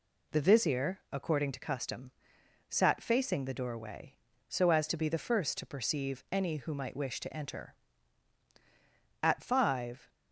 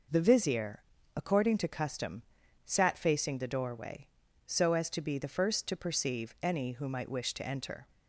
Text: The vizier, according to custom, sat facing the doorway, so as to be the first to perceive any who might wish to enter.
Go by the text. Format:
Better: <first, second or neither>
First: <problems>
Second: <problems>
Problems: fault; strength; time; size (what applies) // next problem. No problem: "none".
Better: second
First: goes on to say "At five"; noticeable; from 9.2 s on; 0.86 s long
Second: none